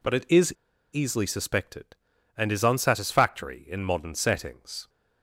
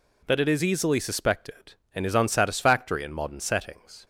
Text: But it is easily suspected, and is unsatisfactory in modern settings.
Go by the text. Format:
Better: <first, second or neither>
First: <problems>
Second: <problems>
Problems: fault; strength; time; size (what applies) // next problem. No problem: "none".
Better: second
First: pauses between "is" and "easily"; at 0.5 s; 0.40 s long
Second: none